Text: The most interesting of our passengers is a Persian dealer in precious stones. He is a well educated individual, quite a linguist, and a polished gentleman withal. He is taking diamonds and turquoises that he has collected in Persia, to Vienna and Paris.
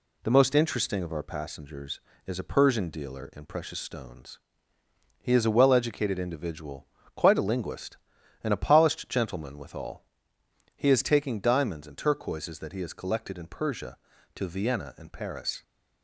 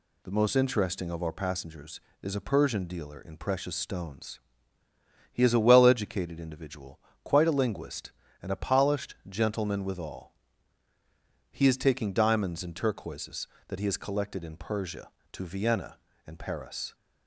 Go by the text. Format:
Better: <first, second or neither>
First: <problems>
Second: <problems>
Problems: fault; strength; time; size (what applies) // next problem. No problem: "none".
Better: neither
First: none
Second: none